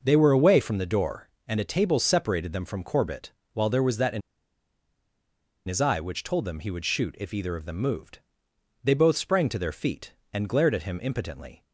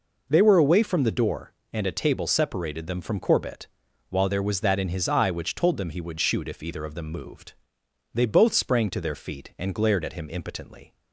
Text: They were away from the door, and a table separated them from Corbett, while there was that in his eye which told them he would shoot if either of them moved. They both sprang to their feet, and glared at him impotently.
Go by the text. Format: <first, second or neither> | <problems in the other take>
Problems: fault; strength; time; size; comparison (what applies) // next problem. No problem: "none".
second | pauses between "in" and "his"; strong; at 4.2 s; 1.4 s long